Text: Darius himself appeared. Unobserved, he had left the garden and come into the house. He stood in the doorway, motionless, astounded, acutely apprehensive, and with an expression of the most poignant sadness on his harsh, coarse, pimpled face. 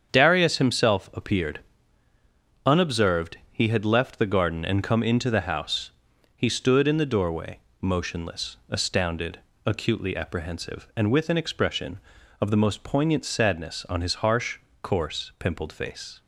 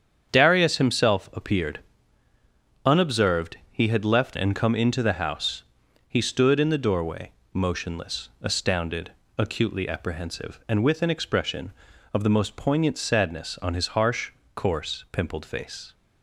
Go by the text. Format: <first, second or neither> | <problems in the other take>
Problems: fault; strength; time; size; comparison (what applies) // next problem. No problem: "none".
first | starts louder than the rest; strong; until 1.3 s; 8 dB; strong in the first // skips "the garden"; at 4.3 s